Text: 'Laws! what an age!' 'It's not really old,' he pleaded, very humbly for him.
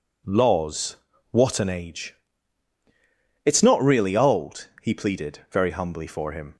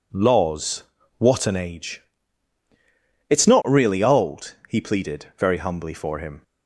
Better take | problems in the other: neither | none

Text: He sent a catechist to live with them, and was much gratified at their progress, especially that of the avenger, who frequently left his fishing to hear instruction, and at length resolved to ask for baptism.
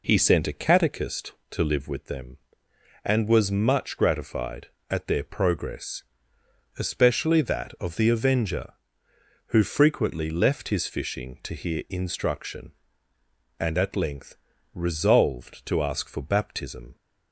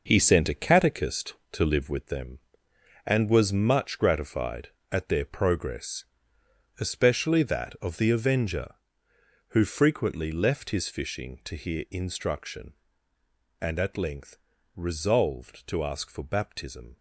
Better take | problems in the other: first | gets quieter; strong; throughout; 9 dB // pauses between "length" and "resolved"; at 14.3 s; 0.38 s long; also in the first

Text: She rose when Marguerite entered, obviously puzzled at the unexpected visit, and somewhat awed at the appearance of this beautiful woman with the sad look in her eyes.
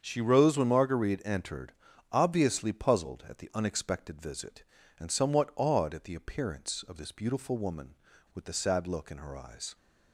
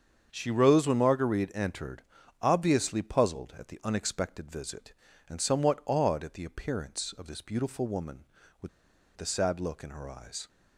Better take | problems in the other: first | starts louder than the rest; until 1.3 s; 7 dB; also in the first // pauses between "with" and "the"; noticeable; at 8.6 s; 0.47 s long

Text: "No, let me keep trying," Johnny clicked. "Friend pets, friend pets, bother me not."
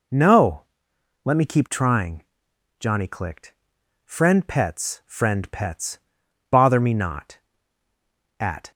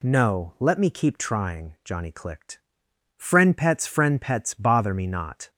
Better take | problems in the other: second | goes on to say "At"; slight; from 8.3 s on; 0.32 s long

